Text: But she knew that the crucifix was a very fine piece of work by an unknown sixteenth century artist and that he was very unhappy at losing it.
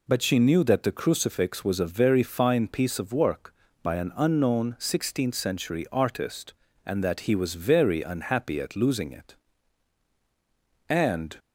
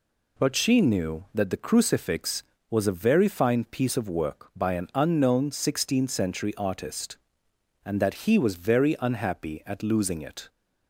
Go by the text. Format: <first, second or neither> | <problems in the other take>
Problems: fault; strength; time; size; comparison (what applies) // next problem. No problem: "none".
second | goes on to say "And"; slight; from 10.8 s on; 0.48 s long